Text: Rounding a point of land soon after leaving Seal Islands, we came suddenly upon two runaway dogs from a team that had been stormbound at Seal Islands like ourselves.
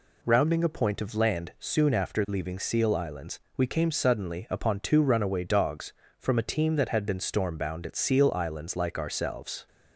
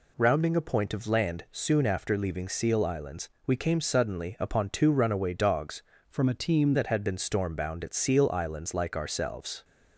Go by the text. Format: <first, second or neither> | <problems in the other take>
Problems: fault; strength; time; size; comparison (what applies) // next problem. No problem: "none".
first | changes voice from "from" to "team"; from 6.0 to 6.7 s; 0.7 s long